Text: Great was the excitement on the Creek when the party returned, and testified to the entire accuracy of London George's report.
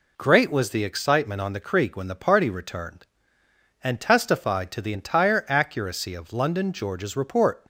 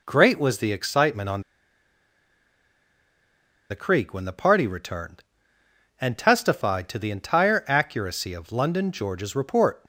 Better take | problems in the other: first | pauses between "on" and "the"; strong; at 1.4 s; 2.2 s long

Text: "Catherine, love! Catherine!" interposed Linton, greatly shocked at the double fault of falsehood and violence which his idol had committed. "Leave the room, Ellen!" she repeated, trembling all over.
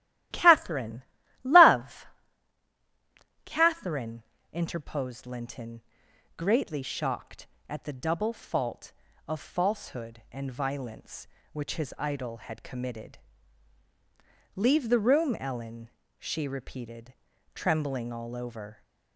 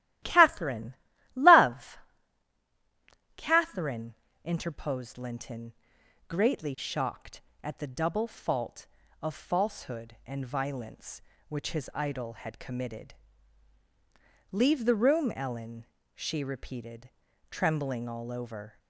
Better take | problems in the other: neither | starts louder than the rest; strong; the same in both

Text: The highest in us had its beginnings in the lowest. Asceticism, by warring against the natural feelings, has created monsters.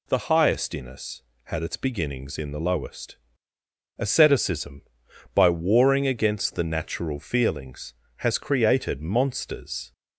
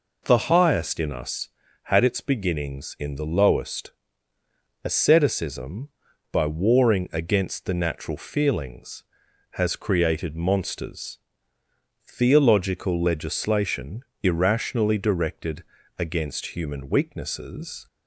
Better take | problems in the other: first | goes on to say "Theological legislation irrationally directed against human weaknesses"; strong; from 12.0 s on; 5.8 s long

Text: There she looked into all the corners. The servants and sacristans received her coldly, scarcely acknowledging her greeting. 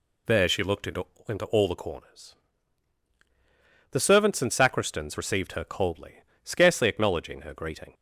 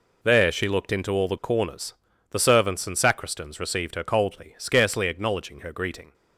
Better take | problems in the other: second | says "into" twice; at 1.2 s

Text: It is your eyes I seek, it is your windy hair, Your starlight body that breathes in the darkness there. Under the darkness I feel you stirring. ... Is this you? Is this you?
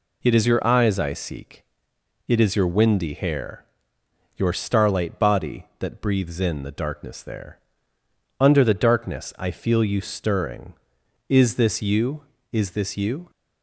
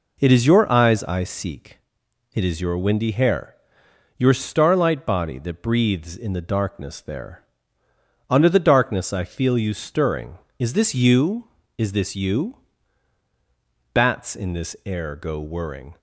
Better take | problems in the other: first | goes on to say "Bats in this air go whirring"; strong; from 13.9 s on; 2.0 s long

